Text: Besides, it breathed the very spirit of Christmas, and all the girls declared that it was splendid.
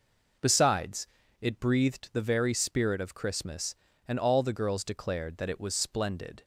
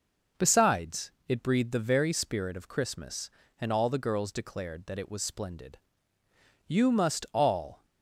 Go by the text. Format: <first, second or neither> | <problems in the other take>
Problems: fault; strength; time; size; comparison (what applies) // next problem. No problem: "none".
first | goes on to say "You must all"; noticeable; from 6.6 s on; 1.1 s long